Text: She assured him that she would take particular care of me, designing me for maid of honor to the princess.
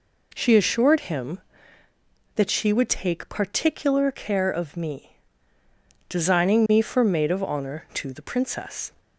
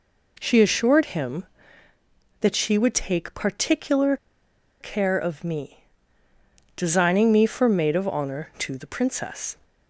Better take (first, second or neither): first